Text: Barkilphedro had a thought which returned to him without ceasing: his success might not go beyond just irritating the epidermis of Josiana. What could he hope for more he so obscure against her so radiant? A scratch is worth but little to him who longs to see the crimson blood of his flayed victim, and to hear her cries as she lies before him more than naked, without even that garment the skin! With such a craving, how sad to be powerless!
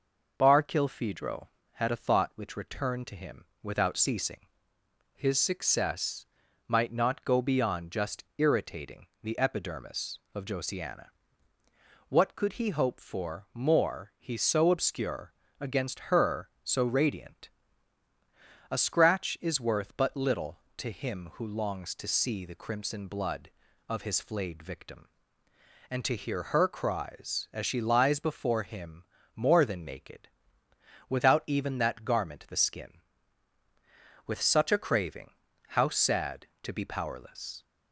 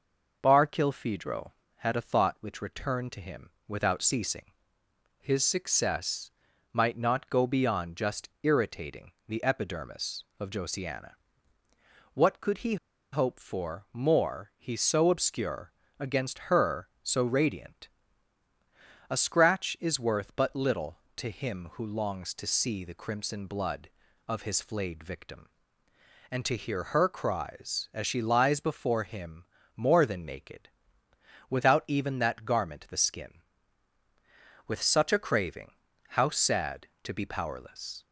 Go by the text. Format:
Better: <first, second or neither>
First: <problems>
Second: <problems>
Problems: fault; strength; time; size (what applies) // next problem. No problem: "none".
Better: first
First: pauses between "him" and "without"; slight; at 3.4 s; 0.16 s long // pauses between "success" and "might"; at 6.2 s; 0.42 s long // pauses between "obscure" and "against"; slight; at 15.3 s; 0.26 s long // pauses between "him" and "more"; slight; at 29.0 s; 0.32 s long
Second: pauses between "him" and "without"; slight; at 3.4 s; 0.16 s long // pauses between "success" and "might"; at 6.2 s; 0.42 s long // pauses between "he" and "hope"; at 12.7 s; 0.36 s long // pauses between "obscure" and "against"; slight; at 15.7 s; 0.26 s long // pauses between "him" and "more"; slight; at 29.4 s; 0.32 s long